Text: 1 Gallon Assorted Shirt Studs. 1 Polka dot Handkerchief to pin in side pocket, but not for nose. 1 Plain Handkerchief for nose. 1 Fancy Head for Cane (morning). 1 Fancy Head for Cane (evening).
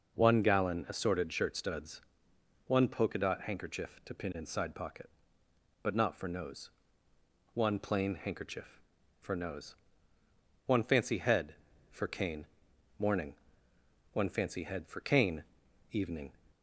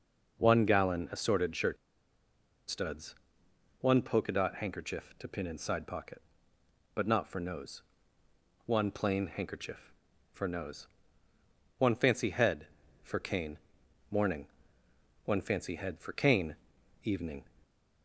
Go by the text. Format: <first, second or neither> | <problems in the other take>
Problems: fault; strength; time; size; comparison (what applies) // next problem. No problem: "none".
first | pauses between "Shirt" and "Studs"; noticeable; at 1.7 s; 0.93 s long